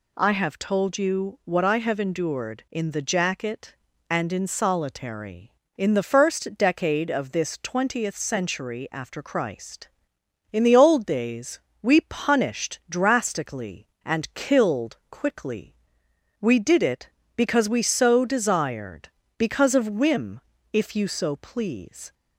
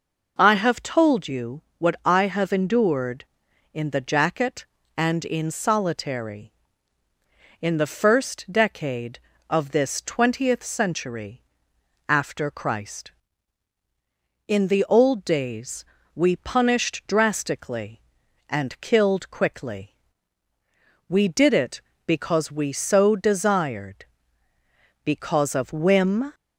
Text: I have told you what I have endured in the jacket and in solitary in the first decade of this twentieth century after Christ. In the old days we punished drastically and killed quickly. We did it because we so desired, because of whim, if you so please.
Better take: first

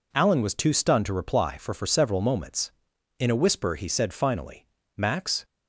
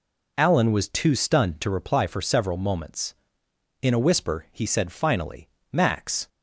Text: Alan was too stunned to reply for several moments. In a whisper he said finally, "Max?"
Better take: second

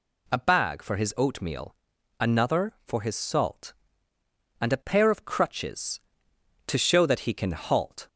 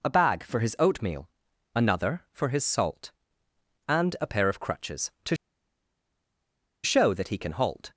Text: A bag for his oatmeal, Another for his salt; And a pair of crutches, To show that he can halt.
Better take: first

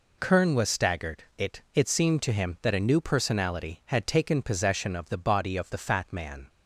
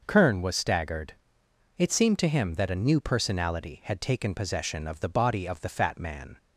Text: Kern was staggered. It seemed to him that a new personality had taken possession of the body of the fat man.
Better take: second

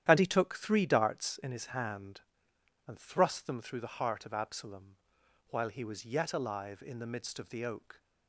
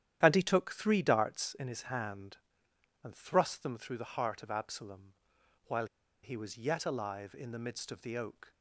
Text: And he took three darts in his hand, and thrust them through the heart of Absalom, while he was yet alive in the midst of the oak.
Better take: first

